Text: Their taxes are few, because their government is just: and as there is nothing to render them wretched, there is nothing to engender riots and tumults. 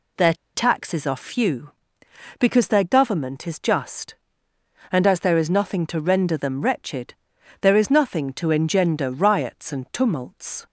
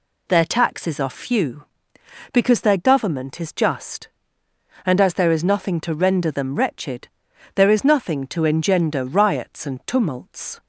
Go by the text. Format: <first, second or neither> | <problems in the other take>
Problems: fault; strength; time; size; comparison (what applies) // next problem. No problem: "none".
second | pauses between "Their" and "taxes"; slight; at 0.3 s; 0.21 s long